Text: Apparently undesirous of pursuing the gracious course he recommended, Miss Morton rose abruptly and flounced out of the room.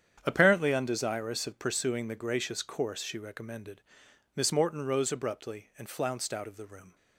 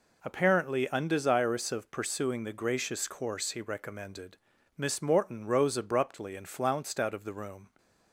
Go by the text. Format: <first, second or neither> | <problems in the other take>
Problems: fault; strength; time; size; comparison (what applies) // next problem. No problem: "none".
second | starts louder than the rest; strong; until 1.2 s; 8.5 dB // says "she" for "he"; at 3.0 s